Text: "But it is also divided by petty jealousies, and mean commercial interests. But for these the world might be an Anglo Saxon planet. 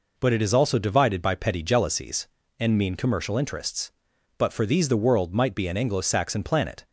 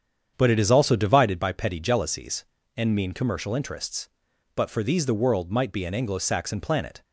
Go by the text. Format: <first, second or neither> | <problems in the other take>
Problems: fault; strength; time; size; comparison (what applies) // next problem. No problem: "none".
first | starts louder than the rest; strong; until 1.4 s; 8 dB